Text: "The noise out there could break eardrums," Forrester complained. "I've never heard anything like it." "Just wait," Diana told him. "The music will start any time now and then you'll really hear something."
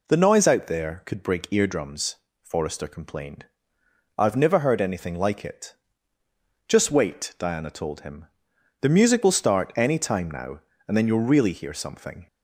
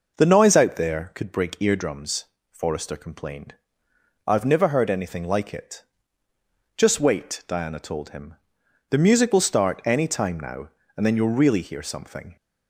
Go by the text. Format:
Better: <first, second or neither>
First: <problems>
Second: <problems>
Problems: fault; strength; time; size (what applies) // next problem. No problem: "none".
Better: first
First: none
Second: starts louder than the rest; noticeable; until 1.2 s; 5.5 dB